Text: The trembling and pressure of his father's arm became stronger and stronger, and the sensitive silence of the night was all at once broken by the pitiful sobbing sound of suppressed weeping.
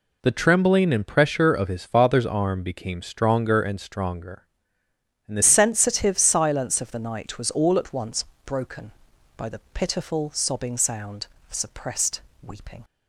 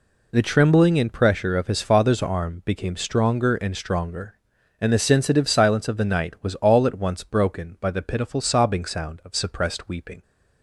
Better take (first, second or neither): second